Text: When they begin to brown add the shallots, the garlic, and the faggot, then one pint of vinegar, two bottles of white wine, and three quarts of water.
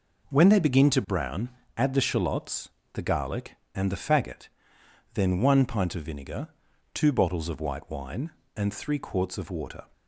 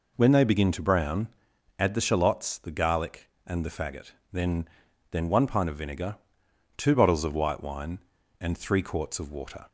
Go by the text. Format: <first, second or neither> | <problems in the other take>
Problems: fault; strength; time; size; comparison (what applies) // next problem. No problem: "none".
first | pauses between "brown" and "add"; noticeable; at 1.2 s; 0.52 s long; slight in the first // says "then" twice; at 5.0 s